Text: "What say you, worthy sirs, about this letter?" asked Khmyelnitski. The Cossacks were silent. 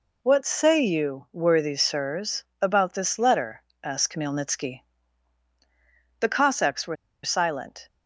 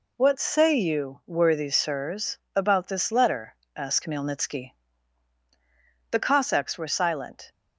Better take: second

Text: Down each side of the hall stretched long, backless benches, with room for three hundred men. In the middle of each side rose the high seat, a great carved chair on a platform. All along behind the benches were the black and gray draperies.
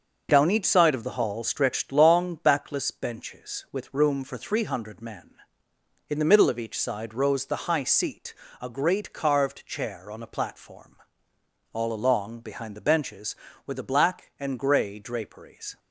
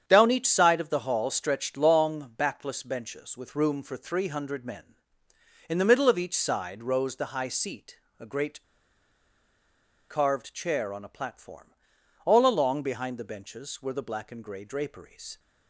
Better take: first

